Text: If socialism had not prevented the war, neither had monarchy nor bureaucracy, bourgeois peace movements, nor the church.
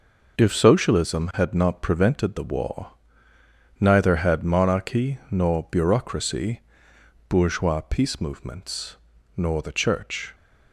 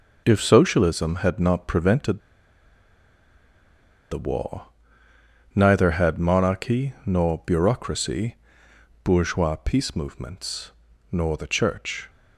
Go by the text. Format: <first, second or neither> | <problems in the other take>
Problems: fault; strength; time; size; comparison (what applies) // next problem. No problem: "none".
first | pauses between "prevented" and "the"; strong; at 2.1 s; 1.9 s long